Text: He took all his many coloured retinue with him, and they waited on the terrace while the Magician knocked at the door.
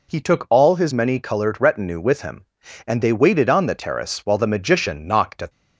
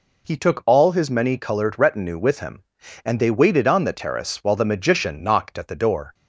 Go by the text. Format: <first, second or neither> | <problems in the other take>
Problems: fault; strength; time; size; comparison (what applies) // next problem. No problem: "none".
second | stops before "the door"; at 5.5 s